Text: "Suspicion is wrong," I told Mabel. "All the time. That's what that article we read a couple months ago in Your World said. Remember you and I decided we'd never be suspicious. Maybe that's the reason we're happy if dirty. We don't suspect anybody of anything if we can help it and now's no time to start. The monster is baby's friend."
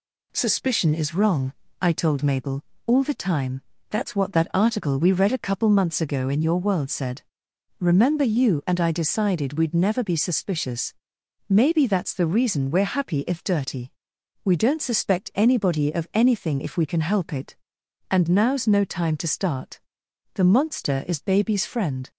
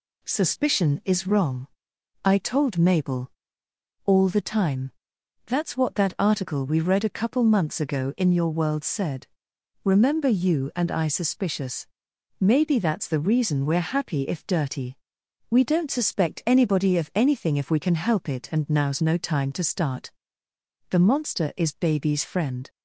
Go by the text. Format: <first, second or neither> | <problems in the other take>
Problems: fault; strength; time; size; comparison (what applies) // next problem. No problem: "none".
first | skips "decided we'd never be"; at 11.0 s